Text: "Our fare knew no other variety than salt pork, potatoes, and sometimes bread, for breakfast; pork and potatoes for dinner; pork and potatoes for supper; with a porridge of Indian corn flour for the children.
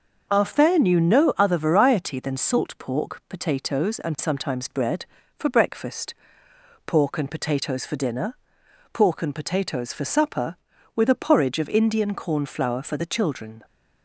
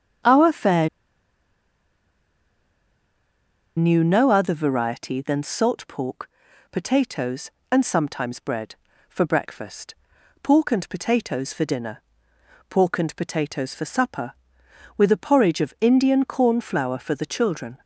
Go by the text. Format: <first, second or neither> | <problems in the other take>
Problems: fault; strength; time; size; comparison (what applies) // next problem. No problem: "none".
first | starts louder than the rest; until 4.1 s; 7 dB // pauses between "fare" and "knew"; strong; at 0.8 s; 2.8 s long